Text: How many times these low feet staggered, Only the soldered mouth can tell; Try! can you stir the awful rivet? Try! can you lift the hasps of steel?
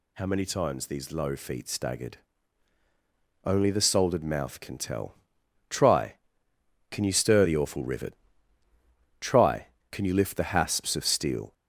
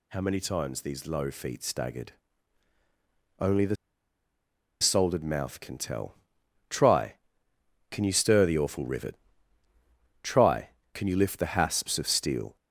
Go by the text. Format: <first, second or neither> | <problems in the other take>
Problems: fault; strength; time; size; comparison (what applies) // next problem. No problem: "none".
first | pauses between "the" and "soldered"; at 3.7 s; 1.0 s long